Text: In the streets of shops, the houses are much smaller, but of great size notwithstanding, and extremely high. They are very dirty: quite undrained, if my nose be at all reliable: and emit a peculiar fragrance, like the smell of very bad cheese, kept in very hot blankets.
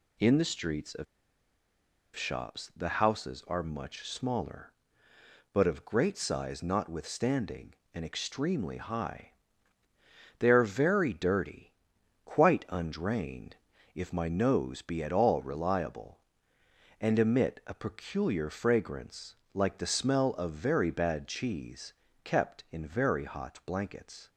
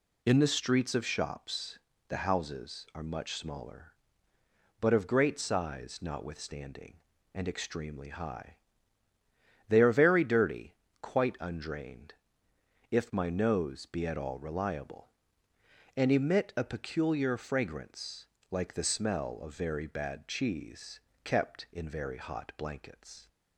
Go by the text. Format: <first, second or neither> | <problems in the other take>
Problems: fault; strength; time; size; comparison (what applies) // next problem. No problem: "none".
second | pauses between "of" and "shops"; at 1.0 s; 1.1 s long